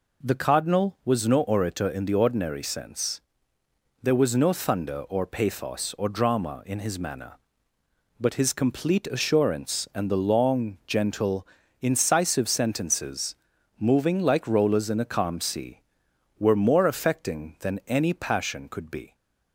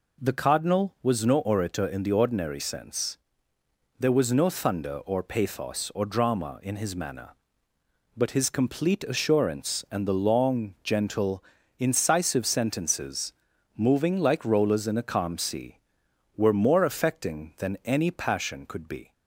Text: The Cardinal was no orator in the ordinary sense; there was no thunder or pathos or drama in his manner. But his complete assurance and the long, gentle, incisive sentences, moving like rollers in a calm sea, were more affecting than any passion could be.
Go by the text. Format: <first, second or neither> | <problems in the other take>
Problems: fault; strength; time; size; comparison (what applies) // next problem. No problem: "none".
neither | none